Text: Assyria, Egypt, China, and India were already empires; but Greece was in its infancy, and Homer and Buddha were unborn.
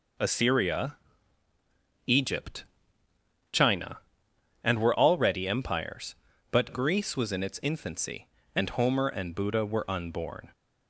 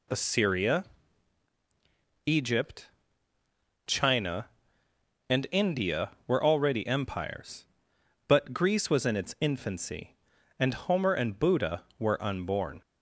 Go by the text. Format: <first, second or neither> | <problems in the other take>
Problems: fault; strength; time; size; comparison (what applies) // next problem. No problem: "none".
second | skips "India"; at 4.7 s